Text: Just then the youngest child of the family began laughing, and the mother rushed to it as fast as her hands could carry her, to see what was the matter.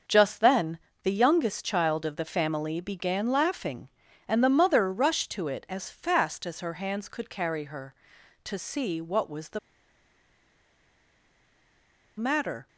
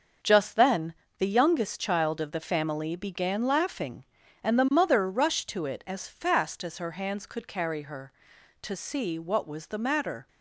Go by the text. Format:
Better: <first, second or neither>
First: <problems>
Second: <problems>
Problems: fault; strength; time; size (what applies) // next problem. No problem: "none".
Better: second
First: starts louder than the rest; until 1.3 s; 6 dB // pauses between "then" and "the"; slight; at 0.7 s; 0.24 s long // pauses between "the" and "matter"; strong; at 9.5 s; 2.6 s long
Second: starts louder than the rest; until 1.4 s; 6 dB // pauses between "then" and "the"; slight; at 0.9 s; 0.24 s long